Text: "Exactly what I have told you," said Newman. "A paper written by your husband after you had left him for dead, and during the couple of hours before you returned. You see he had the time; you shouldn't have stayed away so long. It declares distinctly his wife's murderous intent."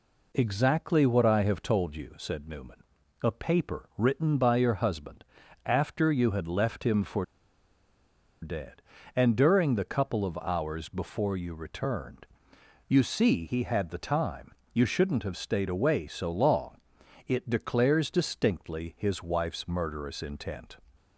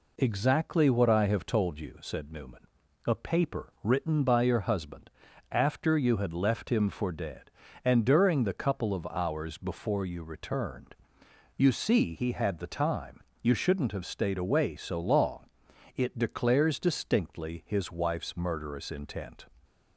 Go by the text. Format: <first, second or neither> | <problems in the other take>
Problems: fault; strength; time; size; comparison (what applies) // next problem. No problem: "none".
second | pauses between "husband" and "after"; at 5.2 s; 0.42 s long; also in the second // pauses between "for" and "dead"; at 7.2 s; 1.1 s long